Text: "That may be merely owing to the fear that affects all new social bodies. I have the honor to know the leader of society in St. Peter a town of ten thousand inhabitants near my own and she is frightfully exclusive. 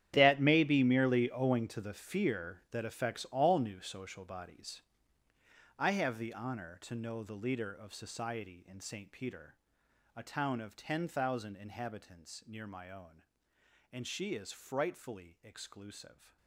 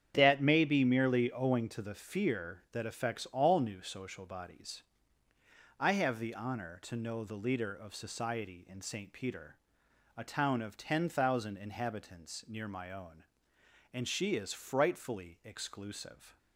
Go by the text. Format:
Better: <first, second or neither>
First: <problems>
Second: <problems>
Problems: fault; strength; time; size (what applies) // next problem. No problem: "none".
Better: second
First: gets quieter; strong; throughout; 16 dB // starts louder than the rest; strong; until 1.1 s; 10.5 dB // pauses between "Peter" and "a"; noticeable; at 9.5 s; 0.58 s long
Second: starts louder than the rest; strong; until 1.1 s; 8.5 dB // pauses between "Peter" and "a"; noticeable; at 9.5 s; 0.58 s long